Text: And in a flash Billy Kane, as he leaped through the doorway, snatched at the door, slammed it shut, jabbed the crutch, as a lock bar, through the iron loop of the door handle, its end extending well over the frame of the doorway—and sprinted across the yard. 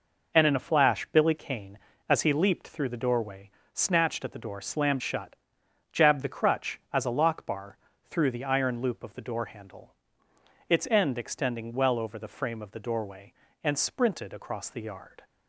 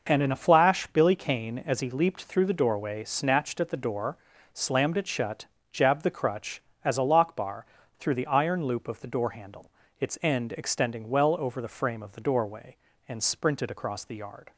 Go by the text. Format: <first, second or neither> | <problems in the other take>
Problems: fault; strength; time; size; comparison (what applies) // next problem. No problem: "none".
second | skips "it"; at 5.0 s